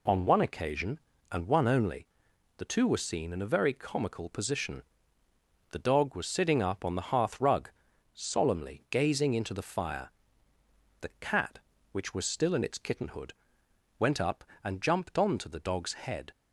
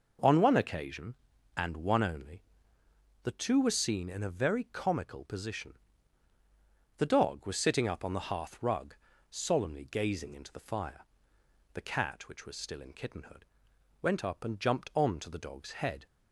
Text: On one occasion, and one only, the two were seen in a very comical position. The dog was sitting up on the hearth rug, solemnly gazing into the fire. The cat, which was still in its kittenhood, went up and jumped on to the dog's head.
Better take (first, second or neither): first